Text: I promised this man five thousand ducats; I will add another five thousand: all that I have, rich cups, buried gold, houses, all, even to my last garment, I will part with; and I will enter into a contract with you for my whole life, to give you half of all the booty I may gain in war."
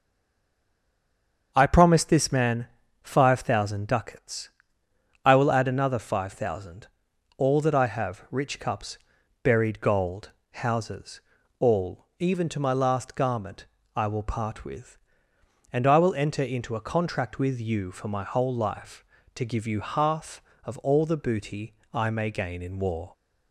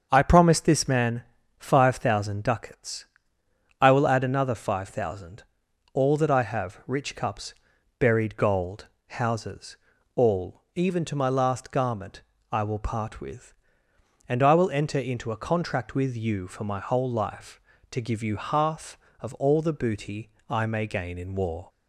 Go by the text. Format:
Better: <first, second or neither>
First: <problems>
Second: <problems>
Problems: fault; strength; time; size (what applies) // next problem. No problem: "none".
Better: second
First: stays silent before the first word; noticeable; until 1.5 s; 1.5 s long // starts louder than the rest; until 2.5 s; 7 dB // pauses between "man" and "five"; slight; at 2.6 s; 0.36 s long // pauses between "booty" and "I"; slight; at 21.7 s; 0.18 s long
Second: starts louder than the rest; until 1.1 s; 7 dB // pauses between "man" and "five"; slight; at 1.2 s; 0.36 s long // pauses between "booty" and "I"; slight; at 20.3 s; 0.18 s long